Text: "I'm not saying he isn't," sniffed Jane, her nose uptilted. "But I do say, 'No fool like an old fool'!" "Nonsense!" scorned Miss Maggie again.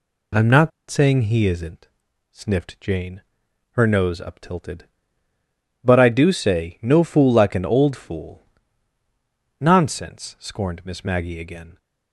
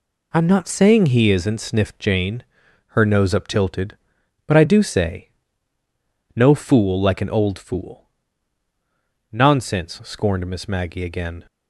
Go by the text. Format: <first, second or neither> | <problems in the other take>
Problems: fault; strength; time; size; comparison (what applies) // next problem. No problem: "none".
second | pauses between "not" and "saying"; slight; at 0.7 s; 0.19 s long